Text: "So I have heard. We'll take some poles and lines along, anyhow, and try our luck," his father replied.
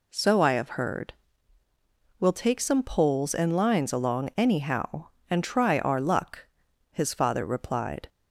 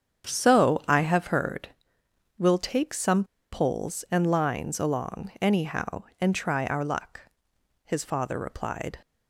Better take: first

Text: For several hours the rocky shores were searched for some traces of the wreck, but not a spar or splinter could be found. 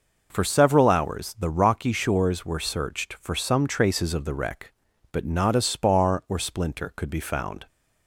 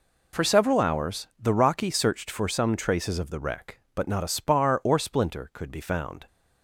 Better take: first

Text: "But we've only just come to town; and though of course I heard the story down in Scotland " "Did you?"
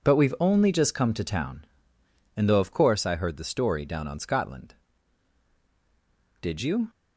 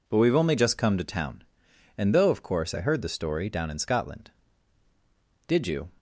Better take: second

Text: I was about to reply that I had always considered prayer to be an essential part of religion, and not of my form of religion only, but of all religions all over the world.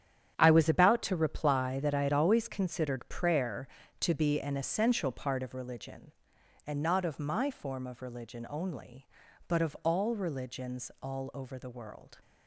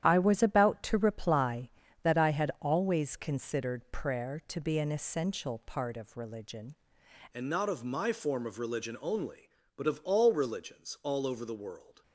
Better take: first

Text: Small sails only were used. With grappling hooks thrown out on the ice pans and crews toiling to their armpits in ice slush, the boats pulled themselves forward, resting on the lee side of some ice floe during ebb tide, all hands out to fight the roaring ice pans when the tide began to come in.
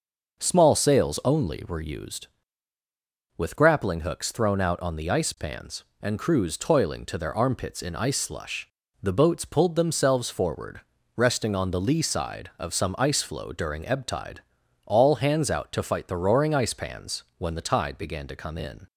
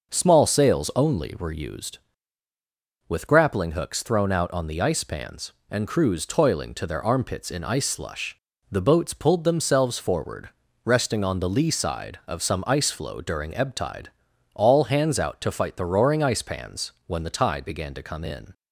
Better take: neither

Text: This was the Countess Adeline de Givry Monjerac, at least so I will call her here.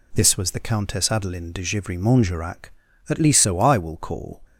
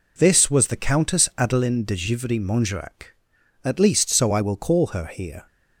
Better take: second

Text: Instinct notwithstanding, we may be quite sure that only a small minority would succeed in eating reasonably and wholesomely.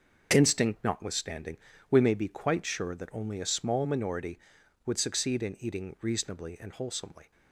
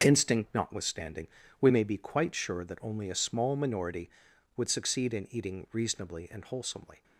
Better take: neither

